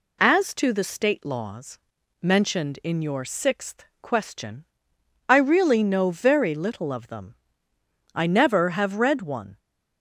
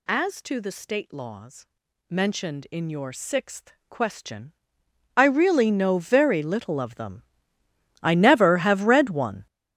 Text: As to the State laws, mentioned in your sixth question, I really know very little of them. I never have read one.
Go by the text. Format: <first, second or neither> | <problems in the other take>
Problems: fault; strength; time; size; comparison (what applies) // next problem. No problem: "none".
first | gets louder; strong; throughout; 12 dB // pauses between "sixth" and "question"; slight; at 3.7 s; 0.16 s long; slight in the first